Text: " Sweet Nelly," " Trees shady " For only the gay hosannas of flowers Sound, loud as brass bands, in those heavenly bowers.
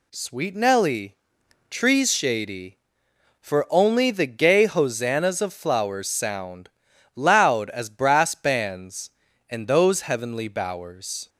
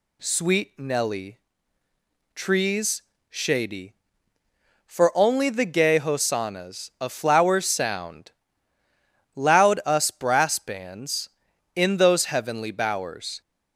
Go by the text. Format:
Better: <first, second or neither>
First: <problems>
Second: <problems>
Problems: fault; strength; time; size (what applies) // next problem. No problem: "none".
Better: first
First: none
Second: pauses between "Trees" and "shady"; slight; at 3.0 s; 0.30 s long // says "us" for "as"; at 9.8 s